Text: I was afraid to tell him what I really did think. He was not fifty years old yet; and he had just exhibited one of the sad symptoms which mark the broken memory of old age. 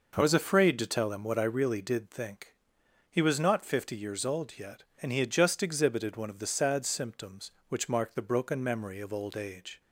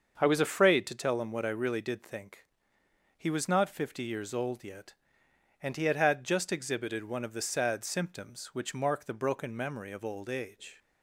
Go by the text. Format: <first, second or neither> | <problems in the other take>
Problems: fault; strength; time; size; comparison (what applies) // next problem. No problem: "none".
first | starts louder than the rest; until 1.1 s; 6.5 dB // says "had" twice; at 5.9 s